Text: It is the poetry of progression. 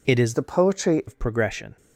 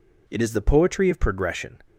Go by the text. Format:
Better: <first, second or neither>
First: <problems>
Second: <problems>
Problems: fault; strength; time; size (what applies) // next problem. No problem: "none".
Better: second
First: changes voice from "the" to "poetry"; from 0.3 to 1.0 s; 0.7 s long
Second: none